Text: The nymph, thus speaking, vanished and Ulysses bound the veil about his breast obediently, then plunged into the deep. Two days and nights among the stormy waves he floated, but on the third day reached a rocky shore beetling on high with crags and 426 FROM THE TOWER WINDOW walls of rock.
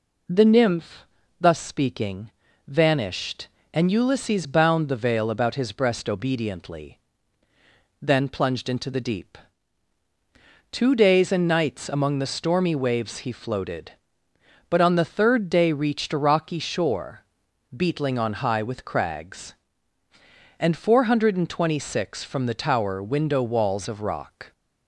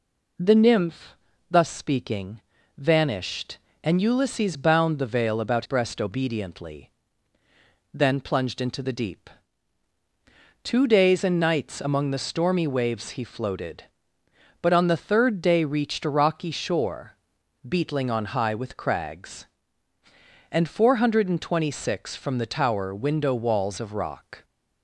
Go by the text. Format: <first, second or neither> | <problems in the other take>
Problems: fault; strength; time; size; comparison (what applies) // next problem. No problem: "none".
first | skips "his"; at 5.6 s // pauses between "shore" and "beetling"; noticeable; at 17.1 s; 0.56 s long; noticeable in the first